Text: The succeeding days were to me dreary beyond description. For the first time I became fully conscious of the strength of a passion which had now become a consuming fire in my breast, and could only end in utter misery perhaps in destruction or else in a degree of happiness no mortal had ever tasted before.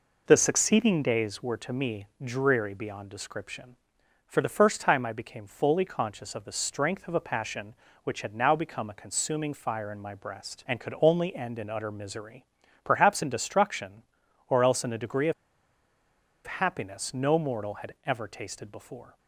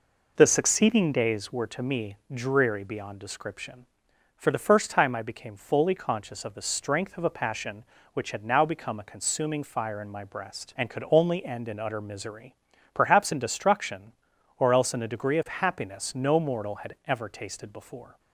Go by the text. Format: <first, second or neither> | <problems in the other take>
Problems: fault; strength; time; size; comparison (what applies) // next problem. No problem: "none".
second | pauses between "misery" and "perhaps"; at 12.4 s; 0.38 s long; also in the second // pauses between "of" and "happiness"; at 15.3 s; 1.1 s long